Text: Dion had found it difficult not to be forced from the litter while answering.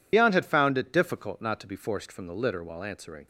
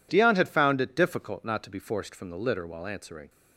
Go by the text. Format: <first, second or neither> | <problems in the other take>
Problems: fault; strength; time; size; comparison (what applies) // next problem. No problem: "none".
second | loses the start of "Dion"; at 0.1 s; 75 ms